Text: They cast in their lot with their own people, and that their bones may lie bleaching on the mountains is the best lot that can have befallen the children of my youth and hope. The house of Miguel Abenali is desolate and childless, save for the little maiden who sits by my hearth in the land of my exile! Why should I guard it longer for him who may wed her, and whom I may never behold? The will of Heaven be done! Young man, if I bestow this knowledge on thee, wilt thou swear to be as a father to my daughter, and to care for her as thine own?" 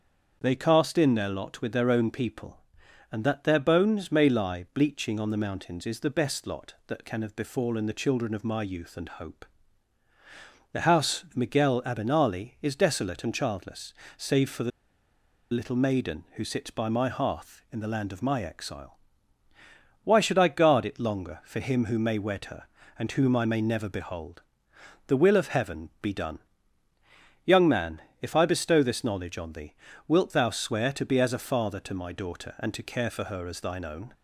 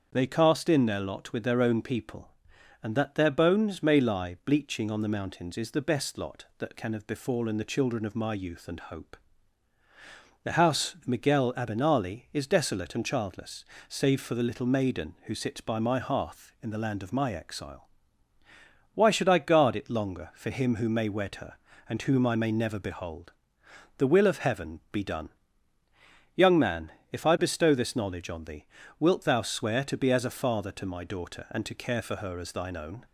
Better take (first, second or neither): second